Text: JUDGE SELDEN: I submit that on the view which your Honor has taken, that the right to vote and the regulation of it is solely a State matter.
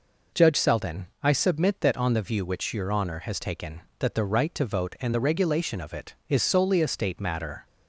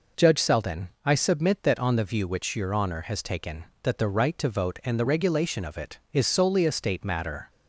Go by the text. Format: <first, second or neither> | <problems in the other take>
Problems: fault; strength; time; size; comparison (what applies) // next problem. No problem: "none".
neither | none